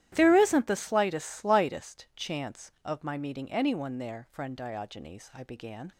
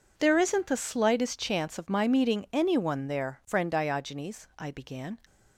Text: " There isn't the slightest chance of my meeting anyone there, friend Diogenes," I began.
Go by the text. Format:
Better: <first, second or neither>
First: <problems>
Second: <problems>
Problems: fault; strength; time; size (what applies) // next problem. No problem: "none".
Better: second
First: starts louder than the rest; strong; until 1.1 s; 13 dB // says "slightest" twice; at 1.2 s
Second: none